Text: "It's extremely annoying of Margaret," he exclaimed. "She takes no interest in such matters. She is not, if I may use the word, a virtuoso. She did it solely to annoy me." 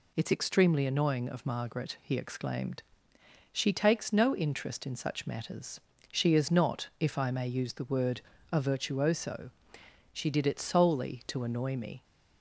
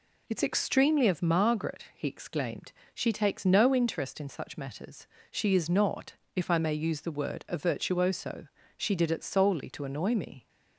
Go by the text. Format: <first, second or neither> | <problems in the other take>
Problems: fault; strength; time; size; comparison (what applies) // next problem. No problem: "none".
first | skips "annoying"; at 1.0 s